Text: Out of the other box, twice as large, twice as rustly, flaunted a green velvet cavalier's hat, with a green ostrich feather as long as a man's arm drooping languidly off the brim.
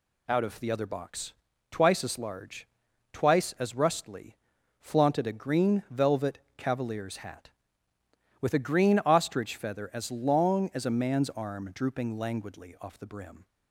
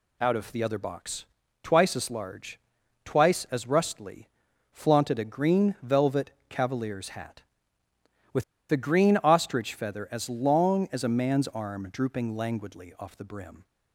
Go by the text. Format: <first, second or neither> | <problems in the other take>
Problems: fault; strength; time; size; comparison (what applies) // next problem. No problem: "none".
first | pauses between "velvet" and "cavalier's"; slight; at 6.2 s; 0.18 s long; slight in the first // pauses between "with" and "a"; slight; at 8.4 s; 0.27 s long